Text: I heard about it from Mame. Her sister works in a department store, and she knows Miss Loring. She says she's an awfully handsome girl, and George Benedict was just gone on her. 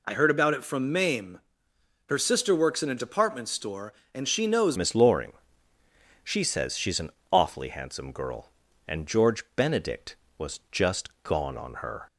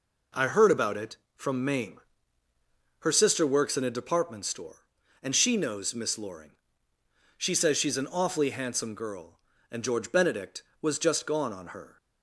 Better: second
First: changes voice at "Miss"; from 4.7 s on; 7.3 s long // pauses between "an" and "awfully"; slight; at 7.1 s; 0.20 s long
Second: none

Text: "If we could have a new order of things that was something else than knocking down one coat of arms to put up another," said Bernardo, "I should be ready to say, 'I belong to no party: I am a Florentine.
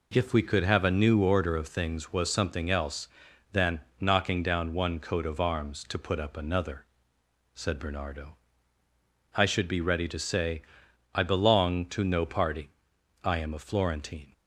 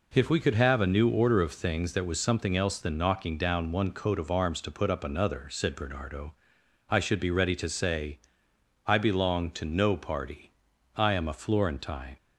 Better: second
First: skips "that"; at 2.1 s // pauses between "than" and "knocking"; slight; at 3.8 s; 0.18 s long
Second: none

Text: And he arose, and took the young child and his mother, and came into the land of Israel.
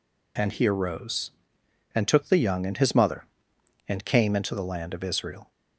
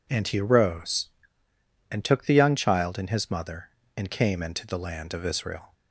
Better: second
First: skips "child"; at 2.6 s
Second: none

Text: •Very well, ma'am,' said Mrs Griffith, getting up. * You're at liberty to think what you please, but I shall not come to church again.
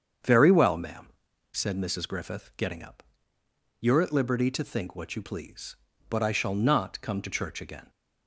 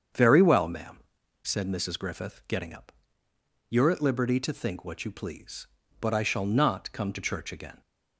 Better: neither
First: starts louder than the rest; strong; until 1.6 s; 7.5 dB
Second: starts louder than the rest; strong; until 1.5 s; 7.5 dB

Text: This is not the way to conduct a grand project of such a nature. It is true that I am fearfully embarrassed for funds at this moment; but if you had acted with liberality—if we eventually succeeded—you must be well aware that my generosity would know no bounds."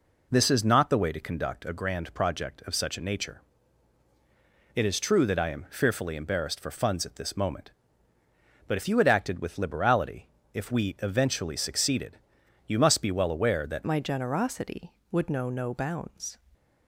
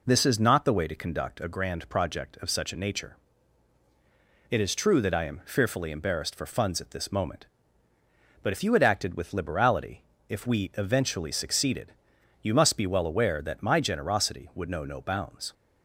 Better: second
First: changes voice at "my"; from 13.8 s on; 2.5 s long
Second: none

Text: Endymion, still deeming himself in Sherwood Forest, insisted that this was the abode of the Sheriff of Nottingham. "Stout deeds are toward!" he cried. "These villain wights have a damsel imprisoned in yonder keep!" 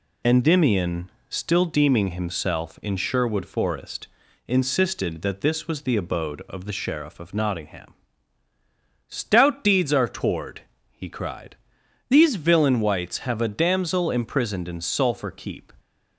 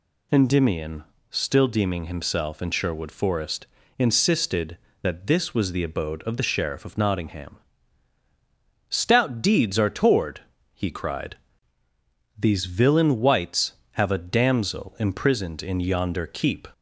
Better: second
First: says "sulphur" for "yonder"; at 14.7 s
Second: none

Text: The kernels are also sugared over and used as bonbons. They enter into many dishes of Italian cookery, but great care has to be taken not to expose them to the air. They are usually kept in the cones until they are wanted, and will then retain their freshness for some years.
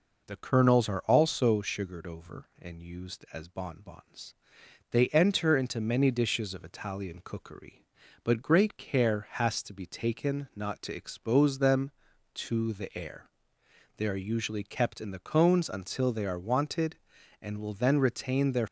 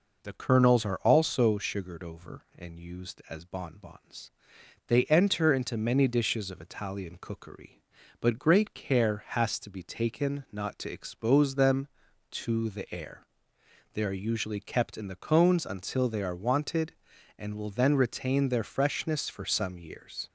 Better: second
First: stops before "freshness for some years"; at 18.6 s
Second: none

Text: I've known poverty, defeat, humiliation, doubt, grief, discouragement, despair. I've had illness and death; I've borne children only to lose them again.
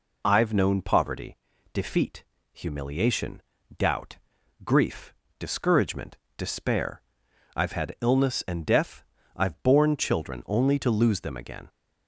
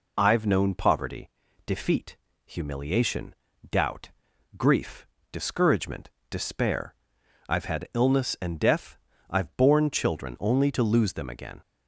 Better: neither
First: none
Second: none

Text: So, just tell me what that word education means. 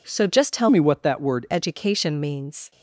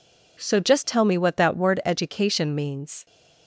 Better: second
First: changes voice from "me" to "word"; from 0.6 to 1.4 s; 0.8 s long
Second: none

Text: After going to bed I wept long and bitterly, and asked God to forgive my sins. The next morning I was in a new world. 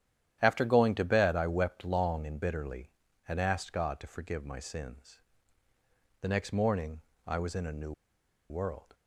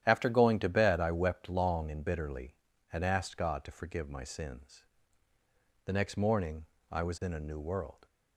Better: second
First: starts louder than the rest; strong; until 1.4 s; 10.5 dB // pauses between "morning" and "I"; slight; at 7.0 s; 0.26 s long // pauses between "new" and "world"; noticeable; at 7.9 s; 0.57 s long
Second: starts louder than the rest; strong; until 1.0 s; 10.5 dB // pauses between "morning" and "I"; slight; at 6.6 s; 0.26 s long

